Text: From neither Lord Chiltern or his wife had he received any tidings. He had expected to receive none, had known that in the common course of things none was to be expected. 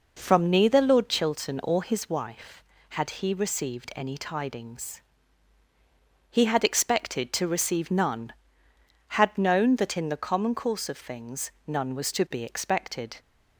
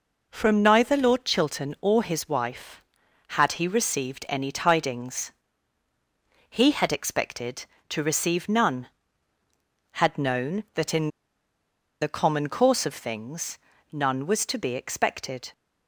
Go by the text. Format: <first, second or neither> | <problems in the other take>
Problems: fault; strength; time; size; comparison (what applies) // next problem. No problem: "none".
first | pauses between "in" and "the"; noticeable; at 11.0 s; 0.93 s long // pauses between "things" and "none"; slight; at 13.5 s; 0.34 s long